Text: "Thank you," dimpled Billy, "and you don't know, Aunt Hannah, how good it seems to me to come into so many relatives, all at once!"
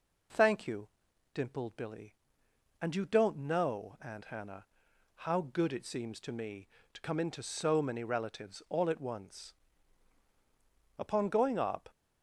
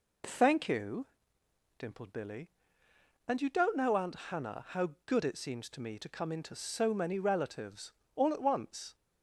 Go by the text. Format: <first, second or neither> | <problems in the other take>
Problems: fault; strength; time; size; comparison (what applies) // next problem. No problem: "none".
second | goes on to say "Upon going up"; noticeable; from 10.9 s on; 0.92 s long